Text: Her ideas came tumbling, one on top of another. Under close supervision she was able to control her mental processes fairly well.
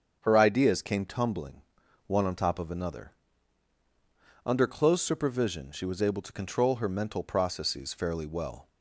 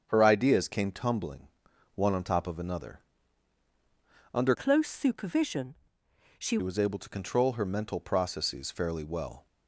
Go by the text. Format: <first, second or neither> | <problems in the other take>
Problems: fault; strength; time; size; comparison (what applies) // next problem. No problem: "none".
first | starts louder than the rest; strong; until 1.0 s; 7 dB; strong in the first // changes voice from "close" to "she"; from 4.5 to 6.5 s; 2.0 s long // pauses between "supervision" and "she"; noticeable; at 5.7 s; 0.64 s long